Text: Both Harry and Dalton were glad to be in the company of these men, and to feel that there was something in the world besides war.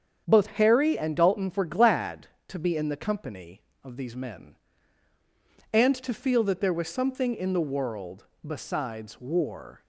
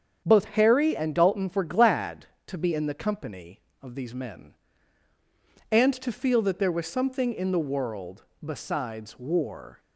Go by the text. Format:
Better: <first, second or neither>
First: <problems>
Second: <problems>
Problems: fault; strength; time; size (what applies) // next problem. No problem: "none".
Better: neither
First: starts louder than the rest; strong; until 1.2 s; 7.5 dB // pauses between "world" and "besides"; slight; at 8.2 s; 0.20 s long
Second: starts louder than the rest; strong; until 1.2 s; 7.5 dB // pauses between "world" and "besides"; slight; at 8.2 s; 0.20 s long